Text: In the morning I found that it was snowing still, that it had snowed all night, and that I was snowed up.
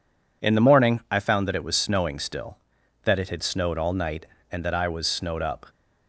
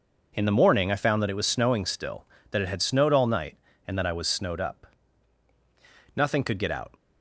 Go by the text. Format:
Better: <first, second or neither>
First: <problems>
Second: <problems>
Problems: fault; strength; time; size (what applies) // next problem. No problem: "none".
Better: first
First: none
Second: starts louder than the rest; strong; until 1.3 s; 7.5 dB // goes on to say "Nothing could get out"; strong; from 4.9 s on; 1.9 s long